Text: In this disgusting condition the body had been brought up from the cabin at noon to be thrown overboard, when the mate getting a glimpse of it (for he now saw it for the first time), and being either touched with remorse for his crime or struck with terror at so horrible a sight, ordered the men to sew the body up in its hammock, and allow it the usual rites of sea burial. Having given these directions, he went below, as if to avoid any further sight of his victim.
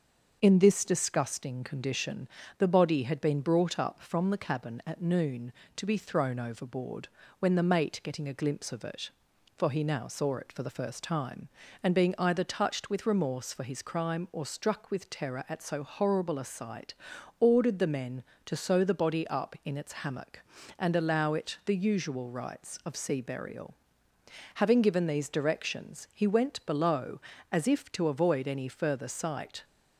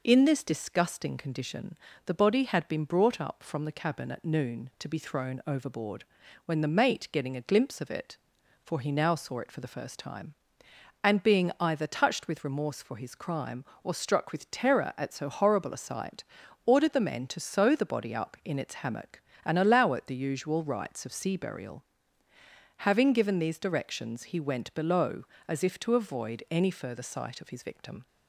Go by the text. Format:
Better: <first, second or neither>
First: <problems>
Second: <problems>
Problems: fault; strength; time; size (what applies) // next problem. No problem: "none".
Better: second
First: starts louder than the rest; until 1.4 s; 6 dB // pauses between "condition" and "the"; slight; at 2.2 s; 0.30 s long // stops before "of his victim"; at 29.6 s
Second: pauses between "condition" and "the"; slight; at 1.7 s; 0.30 s long